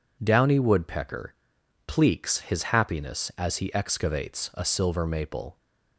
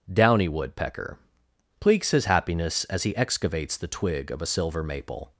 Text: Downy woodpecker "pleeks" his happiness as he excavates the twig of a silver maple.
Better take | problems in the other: second | pauses between "woodpecker" and "pleeks"; noticeable; at 1.3 s; 0.52 s long; noticeable in the second // skips "the twig of"; at 4.5 s

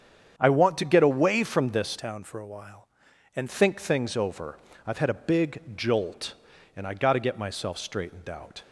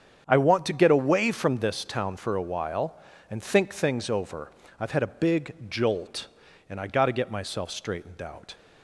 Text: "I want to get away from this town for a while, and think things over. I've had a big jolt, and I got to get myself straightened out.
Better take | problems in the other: second | starts louder than the rest; strong; until 1.4 s; 8 dB; strong in the second // changes voice from "town" to "and"; from 1.9 to 3.4 s; 1.5 s long

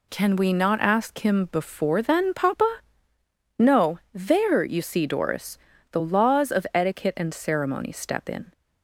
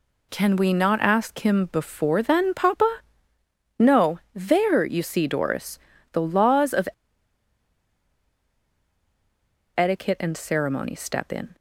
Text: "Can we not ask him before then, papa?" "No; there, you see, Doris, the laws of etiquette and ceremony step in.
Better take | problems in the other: first | pauses between "of" and "etiquette"; strong; at 6.8 s; 2.8 s long

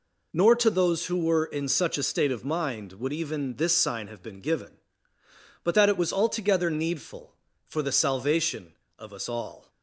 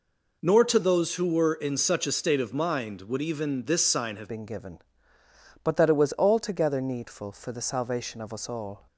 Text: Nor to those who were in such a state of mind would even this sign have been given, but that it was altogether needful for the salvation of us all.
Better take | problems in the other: first | changes voice at "been"; from 4.2 s on; 4.6 s long

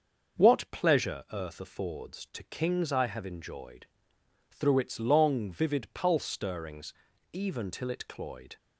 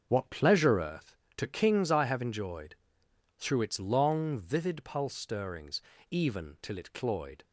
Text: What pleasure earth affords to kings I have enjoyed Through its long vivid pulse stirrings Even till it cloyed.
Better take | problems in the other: first | starts louder than the rest; until 1.1 s; 6.5 dB; also in the first // skips "affords"; at 1.2 s // pauses between "enjoyed" and "Through"; noticeable; at 2.7 s; 0.62 s long; noticeable in the first // pauses between "stirrings" and "Even"; slight; at 5.8 s; 0.30 s long; also in the first

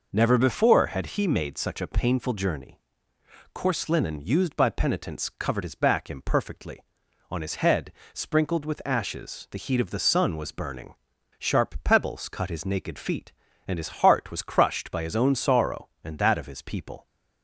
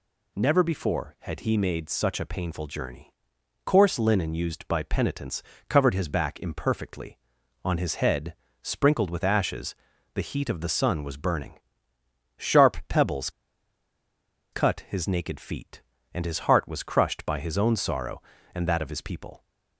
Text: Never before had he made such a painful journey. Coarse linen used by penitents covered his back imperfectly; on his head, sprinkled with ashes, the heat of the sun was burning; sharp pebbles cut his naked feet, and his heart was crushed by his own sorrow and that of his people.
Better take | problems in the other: first | pauses between "penitents" and "covered"; slight; at 5.4 s; 0.24 s long // pauses between "pebbles" and "cut"; at 13.2 s; 1.2 s long

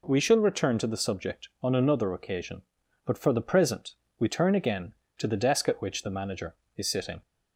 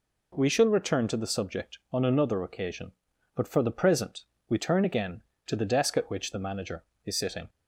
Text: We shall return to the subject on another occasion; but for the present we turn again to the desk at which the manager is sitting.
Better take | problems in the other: neither | pauses between "present" and "we"; slight; the same in both

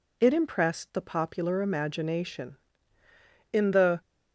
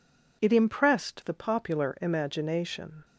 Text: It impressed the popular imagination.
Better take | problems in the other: second | goes on to say "In the"; from 3.5 s on; 0.50 s long

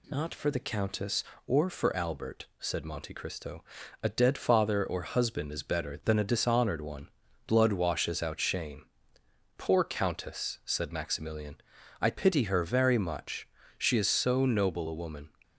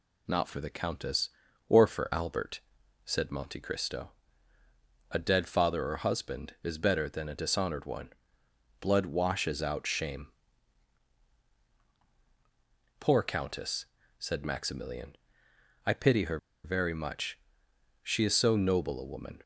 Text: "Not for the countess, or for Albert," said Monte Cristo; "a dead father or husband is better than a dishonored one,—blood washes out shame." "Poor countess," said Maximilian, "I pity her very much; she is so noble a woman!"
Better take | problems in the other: first | pauses between "her" and "very"; slight; at 16.3 s; 0.26 s long

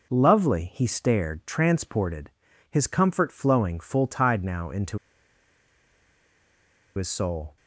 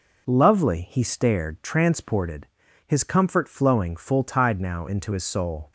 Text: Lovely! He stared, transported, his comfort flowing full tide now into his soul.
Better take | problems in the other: second | pauses between "into" and "his"; strong; at 4.9 s; 1.9 s long

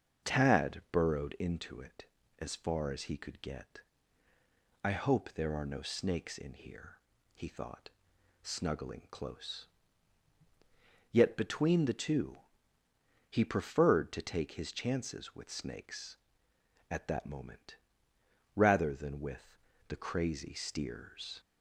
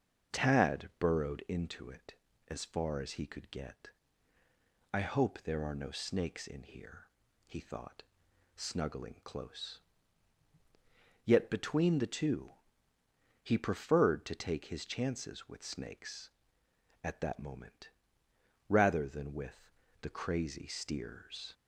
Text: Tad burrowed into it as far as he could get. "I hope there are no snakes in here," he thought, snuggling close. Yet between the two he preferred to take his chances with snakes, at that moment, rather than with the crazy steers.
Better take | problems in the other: neither | starts louder than the rest; the same in both // pauses between "two" and "he"; noticeable; the same in both // pauses between "with" and "the"; slight; the same in both

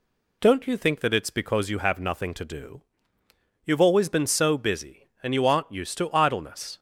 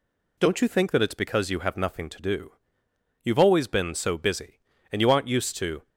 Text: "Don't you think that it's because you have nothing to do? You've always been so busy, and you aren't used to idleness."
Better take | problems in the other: first | stops before "idleness"; at 5.8 s

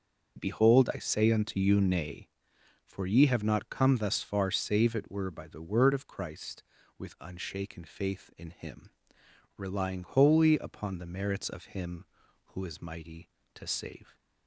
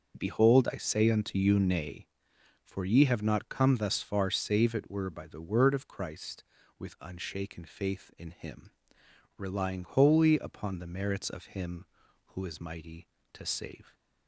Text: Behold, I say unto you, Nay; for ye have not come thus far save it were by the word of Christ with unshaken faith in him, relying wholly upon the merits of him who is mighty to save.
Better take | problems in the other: neither | starts louder than the rest; the same in both

